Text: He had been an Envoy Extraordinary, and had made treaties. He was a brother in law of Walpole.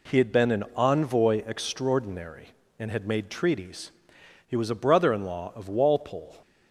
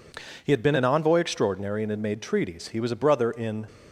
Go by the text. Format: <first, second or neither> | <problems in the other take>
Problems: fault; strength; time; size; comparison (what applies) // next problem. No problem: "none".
first | stops before "law of Walpole"; at 3.6 s